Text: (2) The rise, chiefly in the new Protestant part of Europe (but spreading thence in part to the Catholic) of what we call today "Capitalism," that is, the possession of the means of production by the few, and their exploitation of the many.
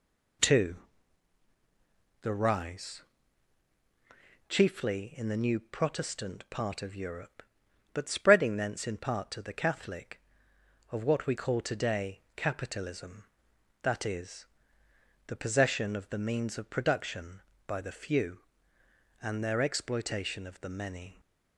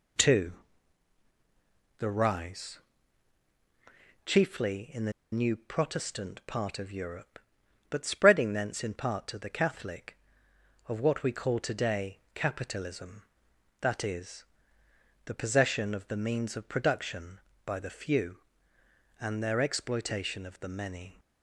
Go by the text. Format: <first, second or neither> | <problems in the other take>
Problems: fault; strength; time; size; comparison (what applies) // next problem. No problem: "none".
first | pauses between "the" and "new"; slight; at 5.1 s; 0.20 s long // pauses between "today" and "Capitalism"; slight; at 12.1 s; 0.16 s long; slight in the first